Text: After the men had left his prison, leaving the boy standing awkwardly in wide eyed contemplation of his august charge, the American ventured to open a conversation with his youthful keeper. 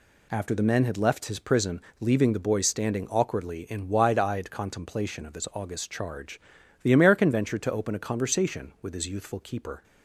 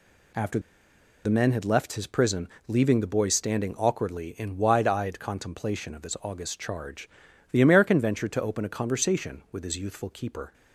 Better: first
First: none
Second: pauses between "After" and "the"; noticeable; at 0.5 s; 0.64 s long

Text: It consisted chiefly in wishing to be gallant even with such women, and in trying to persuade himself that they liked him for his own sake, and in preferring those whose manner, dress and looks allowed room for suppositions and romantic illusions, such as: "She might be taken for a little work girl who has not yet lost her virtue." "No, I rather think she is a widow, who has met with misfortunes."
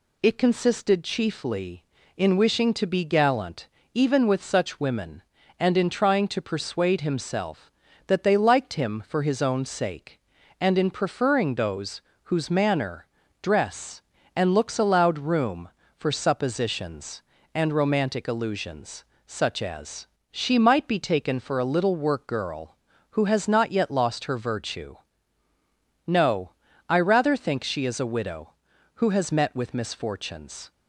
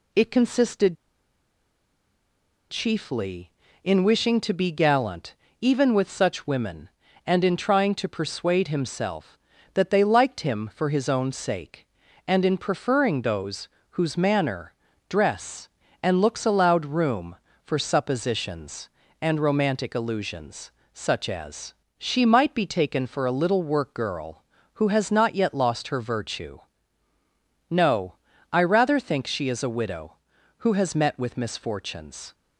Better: first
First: pauses between "gallant" and "even"; slight; at 3.6 s; 0.26 s long // pauses between "those" and "whose"; slight; at 12.0 s; 0.24 s long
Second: pauses between "consisted" and "chiefly"; strong; at 0.9 s; 1.7 s long // pauses between "gallant" and "even"; slight; at 5.3 s; 0.26 s long // pauses between "those" and "whose"; slight; at 13.6 s; 0.24 s long

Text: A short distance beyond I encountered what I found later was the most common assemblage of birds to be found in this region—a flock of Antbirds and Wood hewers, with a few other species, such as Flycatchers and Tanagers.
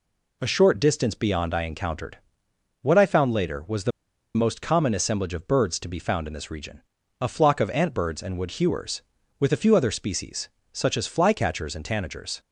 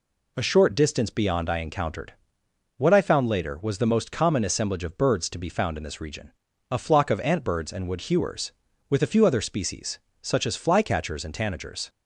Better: second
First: pauses between "encountered" and "what"; noticeable; at 2.1 s; 0.64 s long // pauses between "the" and "most"; at 3.9 s; 0.45 s long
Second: pauses between "encountered" and "what"; noticeable; at 2.1 s; 0.64 s long

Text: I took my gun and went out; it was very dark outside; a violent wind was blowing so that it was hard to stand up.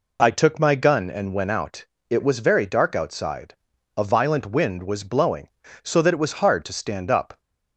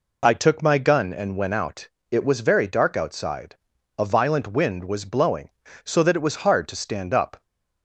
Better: neither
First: none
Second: none

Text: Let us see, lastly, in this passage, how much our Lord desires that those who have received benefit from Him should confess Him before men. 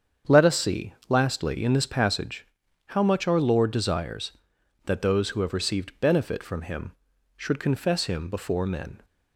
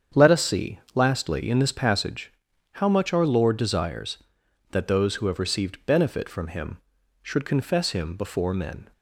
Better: neither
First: starts louder than the rest; strong; until 1.4 s; 7.5 dB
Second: starts louder than the rest; strong; until 1.3 s; 7.5 dB

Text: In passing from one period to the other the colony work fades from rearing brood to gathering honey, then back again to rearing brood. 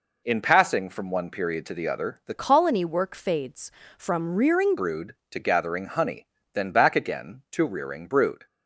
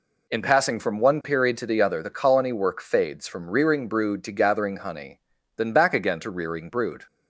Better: second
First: changes voice from "colony" to "rearing"; from 2.3 to 4.7 s; 2.4 s long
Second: none

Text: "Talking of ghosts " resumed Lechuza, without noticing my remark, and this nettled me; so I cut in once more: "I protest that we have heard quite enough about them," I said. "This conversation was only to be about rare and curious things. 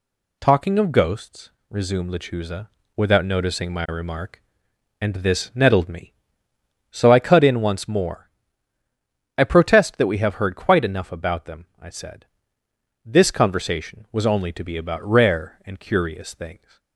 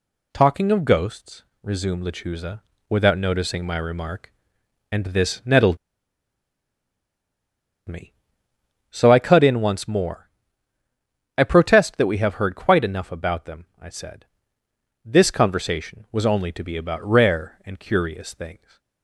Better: first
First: none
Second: pauses between "nettled" and "me"; strong; at 5.7 s; 2.1 s long

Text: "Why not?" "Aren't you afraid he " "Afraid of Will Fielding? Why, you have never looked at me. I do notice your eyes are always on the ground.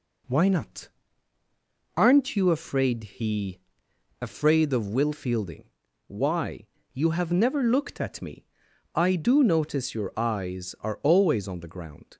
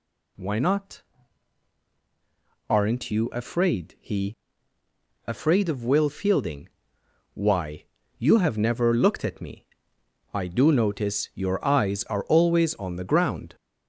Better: first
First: none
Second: gets louder; strong; throughout; 8.5 dB

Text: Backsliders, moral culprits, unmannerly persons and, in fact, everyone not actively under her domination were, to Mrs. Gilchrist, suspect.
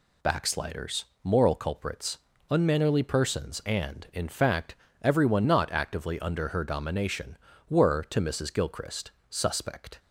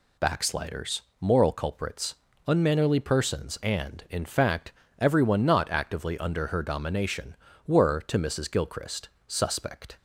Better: neither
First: none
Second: none

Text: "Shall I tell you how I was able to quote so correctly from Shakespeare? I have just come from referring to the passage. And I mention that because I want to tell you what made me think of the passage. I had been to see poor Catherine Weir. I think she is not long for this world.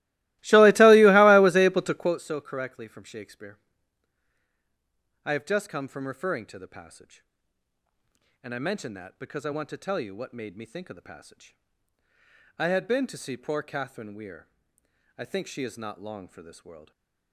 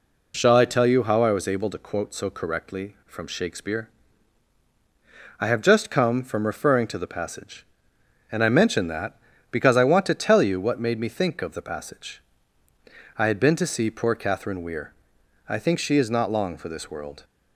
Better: second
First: starts louder than the rest; strong; until 2.2 s; 19 dB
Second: none

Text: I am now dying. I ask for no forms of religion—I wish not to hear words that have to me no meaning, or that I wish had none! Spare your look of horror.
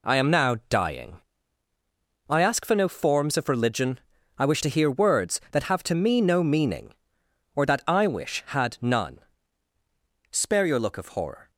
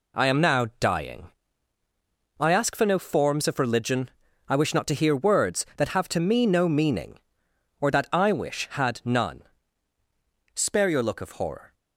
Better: second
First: skips "not"; at 4.6 s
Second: none

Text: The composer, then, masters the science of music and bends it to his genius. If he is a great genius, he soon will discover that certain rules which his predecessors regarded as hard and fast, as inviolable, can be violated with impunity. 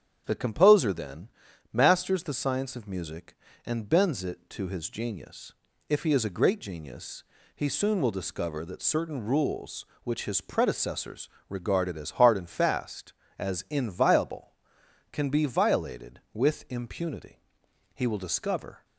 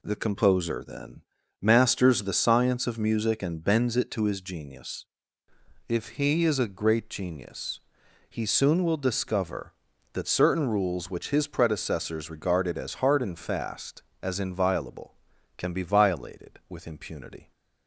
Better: second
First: starts louder than the rest; strong; until 1.2 s; 8.5 dB // pauses between "predecessors" and "regarded"; slight; at 11.2 s; 0.20 s long // goes on to say "He will discover"; noticeable; from 17.9 s on; 0.90 s long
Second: none

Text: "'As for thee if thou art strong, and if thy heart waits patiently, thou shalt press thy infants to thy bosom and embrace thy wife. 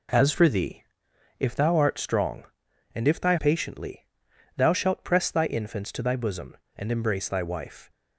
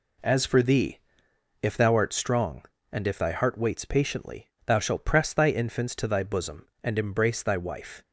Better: second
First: pauses between "thee" and "if"; noticeable; at 0.8 s; 0.54 s long // skips "heart waits"; at 3.3 s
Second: pauses between "thee" and "if"; noticeable; at 0.9 s; 0.62 s long

